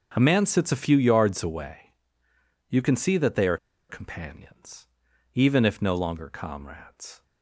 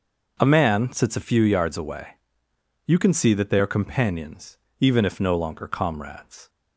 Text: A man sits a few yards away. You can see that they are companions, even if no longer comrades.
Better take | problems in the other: second | starts louder than the rest; until 1.1 s; 6.5 dB // pauses between "are" and "companions"; slight; at 3.5 s; 0.33 s long

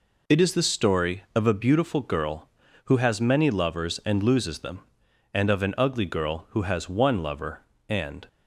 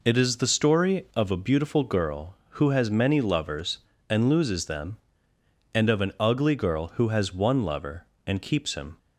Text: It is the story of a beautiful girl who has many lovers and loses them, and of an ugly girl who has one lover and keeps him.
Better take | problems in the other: second | stops before "keeps him"; at 8.2 s

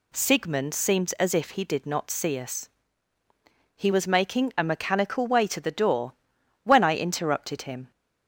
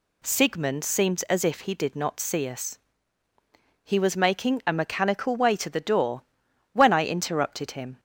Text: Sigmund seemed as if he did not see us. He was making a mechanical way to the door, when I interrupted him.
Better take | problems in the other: neither | none

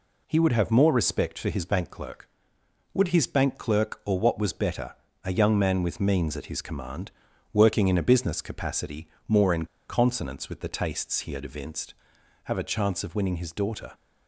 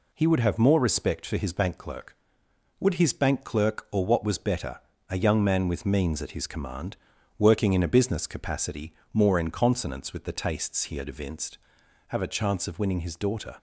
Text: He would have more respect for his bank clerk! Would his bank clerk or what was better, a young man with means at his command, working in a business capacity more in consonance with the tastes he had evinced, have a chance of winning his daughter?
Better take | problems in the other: second | pauses between "capacity" and "more"; slight; at 9.0 s; 0.20 s long; slight in the second // pauses between "in" and "consonance"; slight; at 9.6 s; 0.24 s long

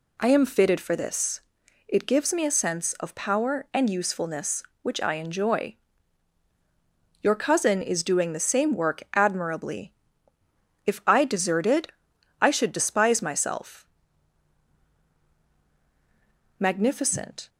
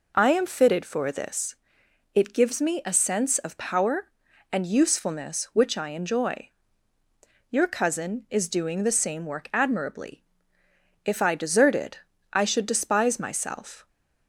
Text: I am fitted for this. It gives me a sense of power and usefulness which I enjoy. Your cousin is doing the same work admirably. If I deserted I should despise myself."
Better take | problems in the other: second | pauses between "deserted" and "I"; noticeable; at 11.8 s; 0.54 s long; slight in the second // goes on to say "Magnificent"; noticeable; from 16.5 s on; 0.90 s long

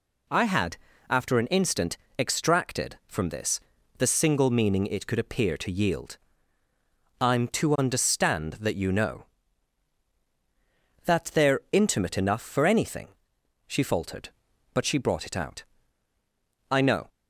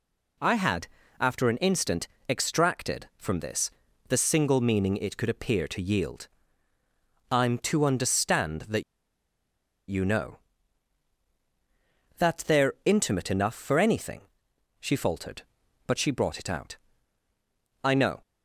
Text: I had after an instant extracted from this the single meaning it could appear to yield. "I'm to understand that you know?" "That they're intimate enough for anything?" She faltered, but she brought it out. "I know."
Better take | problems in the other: first | pauses between "had" and "after"; slight; at 0.8 s; 0.32 s long; slight in the first // pauses between "instant" and "extracted"; slight; at 2.0 s; 0.22 s long; slight in the first // pauses between "this" and "the"; at 3.6 s; 0.38 s long; also in the first // pauses between "that" and "you"; at 8.8 s; 1.0 s long

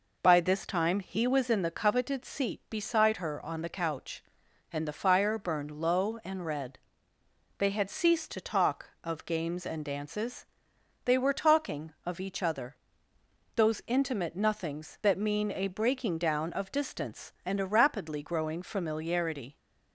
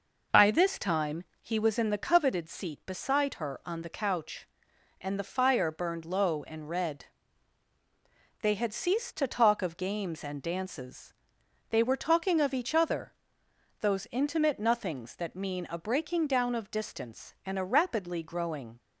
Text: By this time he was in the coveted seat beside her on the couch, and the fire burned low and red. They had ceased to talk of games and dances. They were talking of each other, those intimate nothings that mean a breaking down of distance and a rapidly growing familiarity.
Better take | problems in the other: first | pauses between "time" and "he"; slight; at 1.2 s; 0.18 s long // stops before "familiarity"; at 18.7 s

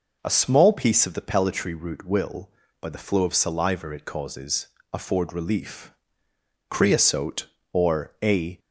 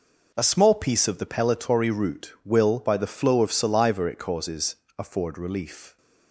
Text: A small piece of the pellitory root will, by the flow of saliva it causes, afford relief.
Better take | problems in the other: second | goes on to say "Creosote or a"; strong; from 6.7 s on; 1.8 s long

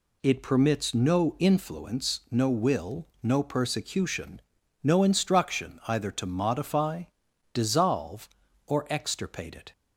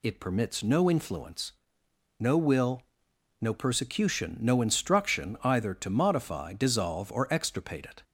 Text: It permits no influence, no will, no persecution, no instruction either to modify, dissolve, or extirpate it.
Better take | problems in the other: neither | none

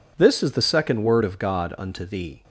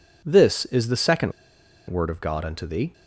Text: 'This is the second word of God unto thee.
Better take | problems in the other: first | pauses between "second" and "word"; noticeable; at 1.3 s; 0.56 s long

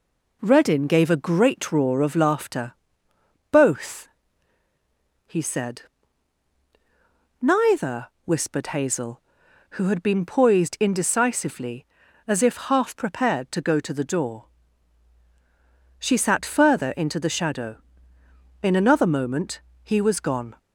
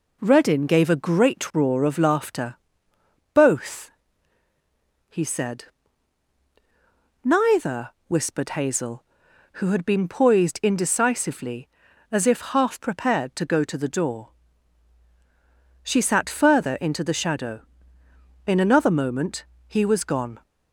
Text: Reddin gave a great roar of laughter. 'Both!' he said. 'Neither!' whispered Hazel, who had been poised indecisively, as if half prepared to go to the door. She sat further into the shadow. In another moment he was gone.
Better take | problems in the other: neither | pauses between "moment" and "he"; slight; the same in both

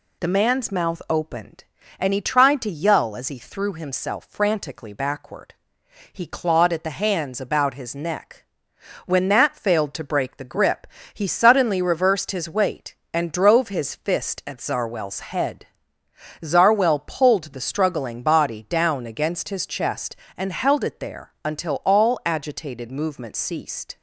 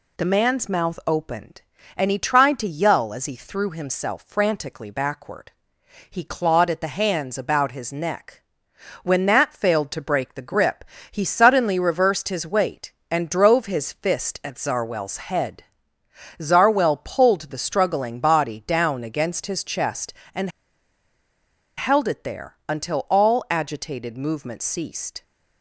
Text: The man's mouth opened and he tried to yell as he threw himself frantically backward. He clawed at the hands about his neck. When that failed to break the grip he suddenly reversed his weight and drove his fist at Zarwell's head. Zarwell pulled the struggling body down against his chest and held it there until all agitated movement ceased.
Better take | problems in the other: first | pauses between "grip" and "he"; slight; at 10.8 s; 0.26 s long; slight in the first // pauses between "and" and "held"; strong; at 20.4 s; 1.2 s long

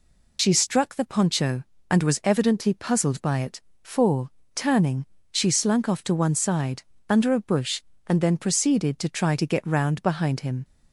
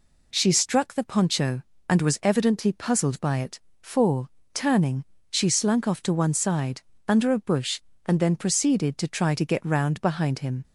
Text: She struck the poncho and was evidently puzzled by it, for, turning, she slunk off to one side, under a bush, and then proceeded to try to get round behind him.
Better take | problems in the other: second | loses the start of "She"; at 0.3 s; 50 ms

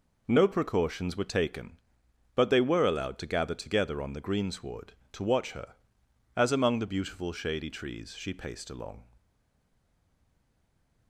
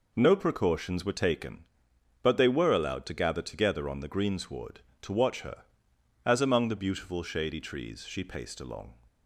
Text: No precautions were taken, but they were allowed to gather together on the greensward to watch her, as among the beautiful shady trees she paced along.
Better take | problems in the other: second | stays silent after the last word; noticeable; from 9.1 s on; 1.9 s long

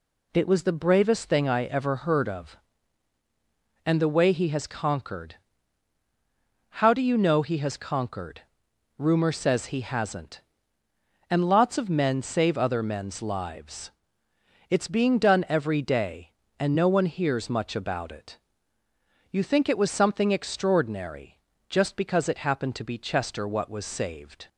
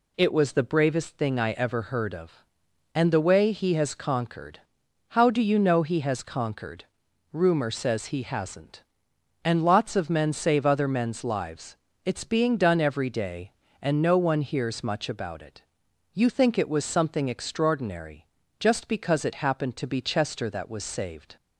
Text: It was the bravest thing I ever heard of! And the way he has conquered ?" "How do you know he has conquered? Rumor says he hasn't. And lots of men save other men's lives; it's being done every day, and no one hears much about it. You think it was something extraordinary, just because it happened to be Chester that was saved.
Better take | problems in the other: second | says "what" for "that"; at 23.4 s

